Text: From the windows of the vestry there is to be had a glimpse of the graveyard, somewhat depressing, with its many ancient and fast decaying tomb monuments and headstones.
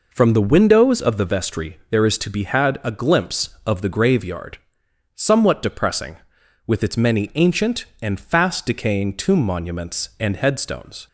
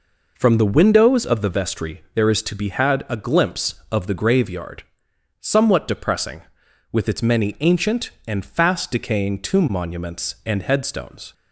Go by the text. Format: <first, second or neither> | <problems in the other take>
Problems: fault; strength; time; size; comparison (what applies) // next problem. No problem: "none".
neither | none